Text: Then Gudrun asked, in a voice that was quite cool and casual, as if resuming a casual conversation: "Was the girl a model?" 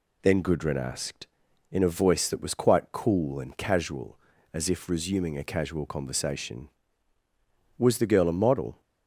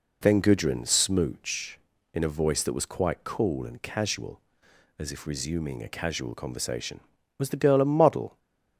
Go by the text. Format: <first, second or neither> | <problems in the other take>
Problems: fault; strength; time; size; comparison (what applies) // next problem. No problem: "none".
first | says "smooch" for "asked"; at 0.8 s // stays silent after the last word; slight; from 8.2 s on; 0.5 s long